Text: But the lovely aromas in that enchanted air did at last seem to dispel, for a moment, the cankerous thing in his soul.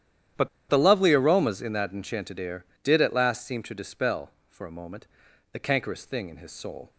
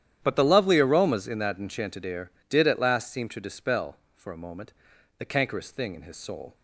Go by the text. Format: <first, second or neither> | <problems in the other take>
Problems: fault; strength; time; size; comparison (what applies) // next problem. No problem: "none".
second | starts louder than the rest; strong; until 1.5 s; 10.5 dB; strong in the second // pauses between "But" and "the"; slight; at 0.4 s; 0.21 s long